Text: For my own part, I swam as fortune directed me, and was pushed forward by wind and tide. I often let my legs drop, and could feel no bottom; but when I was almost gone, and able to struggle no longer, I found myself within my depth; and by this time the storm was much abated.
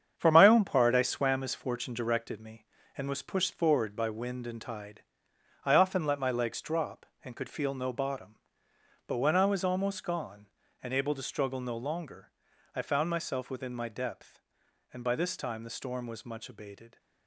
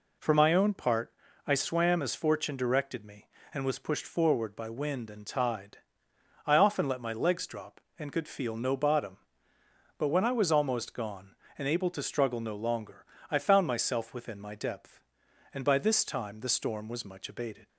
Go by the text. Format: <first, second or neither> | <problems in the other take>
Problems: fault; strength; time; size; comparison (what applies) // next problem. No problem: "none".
second | gets quieter; strong; throughout; 8 dB